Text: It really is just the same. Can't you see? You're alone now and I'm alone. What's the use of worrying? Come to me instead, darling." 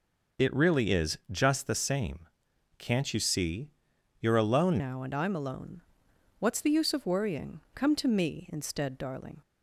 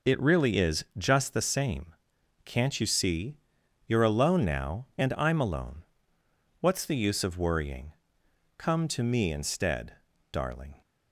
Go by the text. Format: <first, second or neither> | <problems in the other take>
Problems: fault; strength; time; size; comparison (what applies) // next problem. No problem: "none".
second | changes voice at "now"; from 4.7 s on; 4.7 s long